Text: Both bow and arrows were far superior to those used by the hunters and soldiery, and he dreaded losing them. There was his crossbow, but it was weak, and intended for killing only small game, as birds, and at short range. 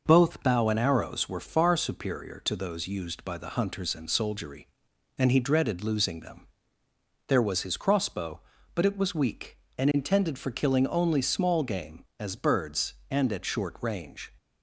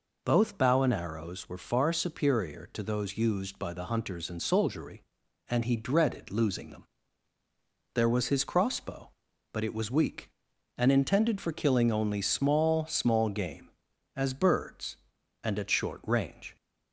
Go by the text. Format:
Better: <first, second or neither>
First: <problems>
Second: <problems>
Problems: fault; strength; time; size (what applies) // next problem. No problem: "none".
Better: first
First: none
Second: says "small" twice; at 12.8 s